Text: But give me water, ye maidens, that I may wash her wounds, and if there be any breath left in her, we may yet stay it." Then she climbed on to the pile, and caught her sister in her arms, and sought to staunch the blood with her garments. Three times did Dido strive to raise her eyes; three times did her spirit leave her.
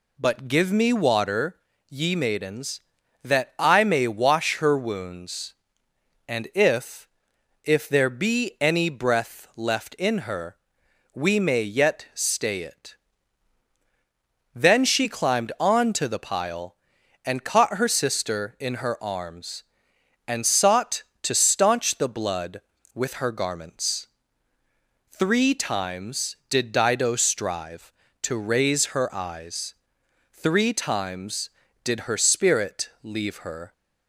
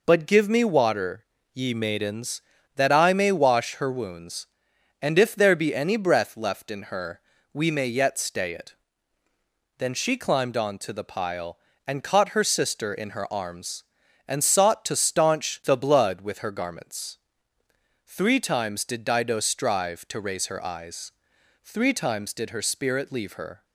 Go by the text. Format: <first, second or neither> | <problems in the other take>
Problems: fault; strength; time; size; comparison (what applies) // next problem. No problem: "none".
second | says "if" twice; at 7.6 s